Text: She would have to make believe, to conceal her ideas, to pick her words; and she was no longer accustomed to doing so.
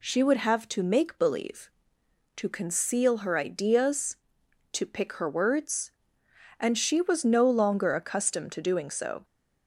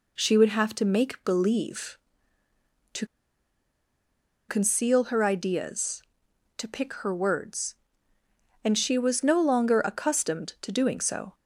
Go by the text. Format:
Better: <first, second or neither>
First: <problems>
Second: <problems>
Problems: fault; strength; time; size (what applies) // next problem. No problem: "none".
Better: first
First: none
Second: pauses between "to" and "conceal"; strong; at 3.0 s; 1.4 s long